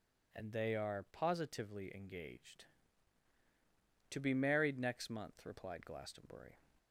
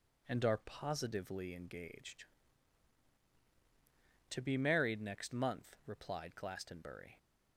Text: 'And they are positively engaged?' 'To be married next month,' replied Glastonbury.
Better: first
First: none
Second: skips "they"; at 0.4 s

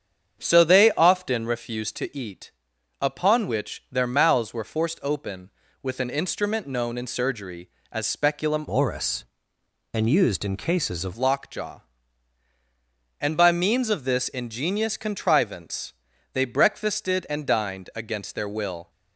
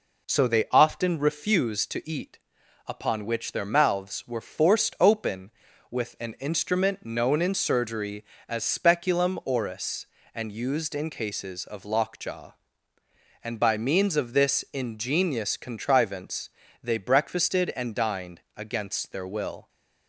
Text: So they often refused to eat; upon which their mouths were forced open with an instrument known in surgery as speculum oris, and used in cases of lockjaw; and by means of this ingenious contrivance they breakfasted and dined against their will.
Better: second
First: starts louder than the rest; strong; until 1.4 s; 8 dB // changes voice from "oris" to "of"; from 8.6 to 11.1 s; 2.5 s long // pauses between "contrivance" and "they"; at 15.9 s; 0.40 s long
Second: pauses between "contrivance" and "they"; slight; at 16.4 s; 0.34 s long

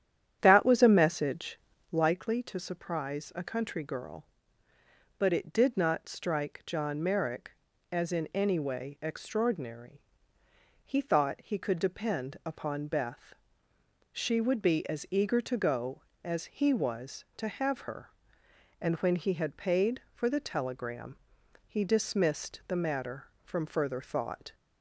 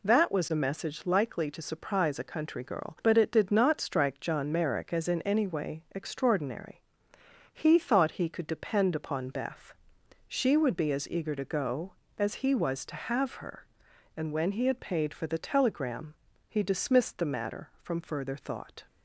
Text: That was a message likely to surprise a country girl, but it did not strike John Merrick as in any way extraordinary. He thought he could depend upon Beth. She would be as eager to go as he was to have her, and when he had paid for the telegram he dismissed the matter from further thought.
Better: second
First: starts louder than the rest; strong; until 2.1 s; 9.5 dB // pauses between "message" and "likely"; slight; at 1.5 s; 0.34 s long // pauses between "telegram" and "he"; noticeable; at 21.1 s; 0.50 s long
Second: pauses between "telegram" and "he"; slight; at 16.1 s; 0.34 s long

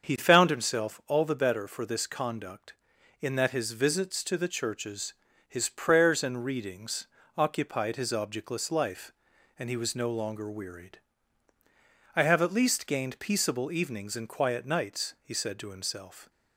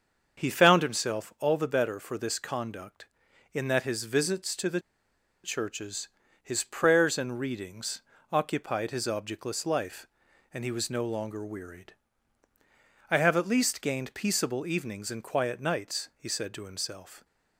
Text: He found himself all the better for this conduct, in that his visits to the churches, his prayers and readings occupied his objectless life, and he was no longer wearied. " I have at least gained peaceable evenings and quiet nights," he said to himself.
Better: first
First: starts louder than the rest; until 1.1 s; 7 dB // pauses between "readings" and "occupied"; slight; at 7.0 s; 0.28 s long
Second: starts louder than the rest; until 1.4 s; 7 dB // pauses between "the" and "churches"; noticeable; at 4.7 s; 0.65 s long // pauses between "readings" and "occupied"; slight; at 8.0 s; 0.28 s long

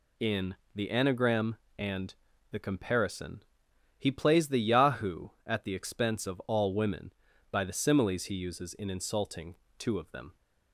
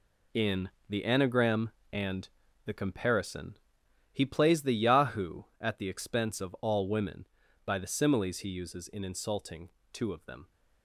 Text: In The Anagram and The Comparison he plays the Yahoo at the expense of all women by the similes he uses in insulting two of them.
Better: first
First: pauses between "In" and "The"; slight; at 0.5 s; 0.20 s long // pauses between "and" and "The"; slight; at 2.1 s; 0.36 s long // pauses between "Comparison" and "he"; noticeable; at 3.4 s; 0.56 s long // pauses between "insulting" and "two"; slight; at 9.5 s; 0.22 s long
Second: gets quieter; strong; throughout; 10.5 dB // pauses between "In" and "The"; slight; at 0.6 s; 0.20 s long // pauses between "and" and "The"; slight; at 2.2 s; 0.36 s long // pauses between "Comparison" and "he"; noticeable; at 3.5 s; 0.56 s long // pauses between "insulting" and "two"; slight; at 9.7 s; 0.22 s long

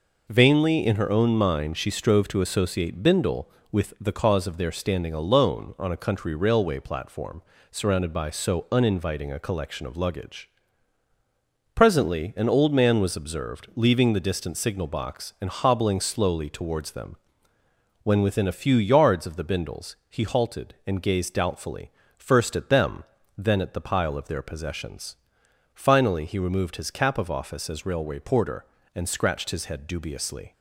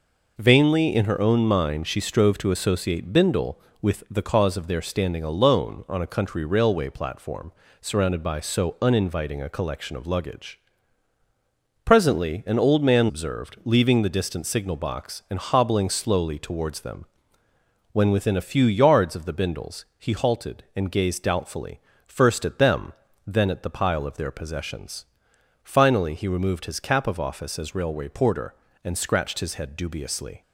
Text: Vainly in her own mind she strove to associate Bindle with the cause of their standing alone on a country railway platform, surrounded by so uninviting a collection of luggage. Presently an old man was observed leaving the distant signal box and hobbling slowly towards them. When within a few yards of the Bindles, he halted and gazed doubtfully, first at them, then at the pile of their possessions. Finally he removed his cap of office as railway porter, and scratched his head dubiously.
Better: first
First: none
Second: skips "was"; at 13.0 s

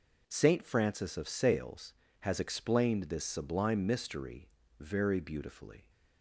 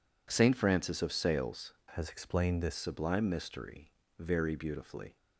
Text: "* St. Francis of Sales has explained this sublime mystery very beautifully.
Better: first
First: pauses between "mystery" and "very"; slight; at 4.4 s; 0.31 s long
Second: changes voice from "has" to "this"; from 1.9 to 2.7 s; 0.8 s long // pauses between "mystery" and "very"; slight; at 3.9 s; 0.26 s long

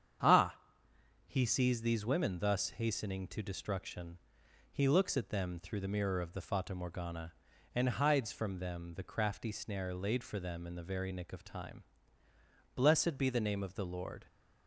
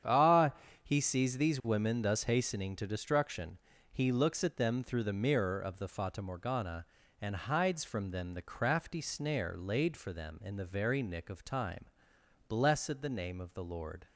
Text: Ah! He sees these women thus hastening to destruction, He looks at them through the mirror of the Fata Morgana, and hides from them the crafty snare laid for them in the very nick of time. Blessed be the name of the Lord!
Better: first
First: starts louder than the rest; strong; until 1.9 s; 8 dB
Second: starts louder than the rest; strong; until 1.3 s; 8.5 dB // skips "be"; at 13.0 s

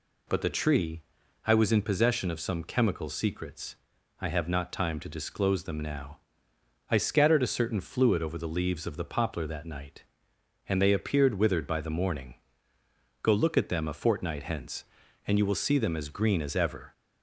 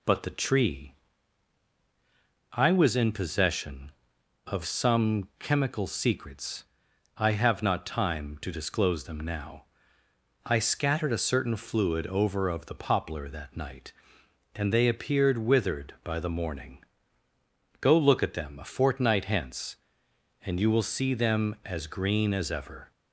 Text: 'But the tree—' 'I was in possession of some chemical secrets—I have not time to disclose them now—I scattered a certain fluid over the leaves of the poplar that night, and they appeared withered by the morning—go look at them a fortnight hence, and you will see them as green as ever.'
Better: first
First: none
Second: skips "the leaves"; at 12.4 s

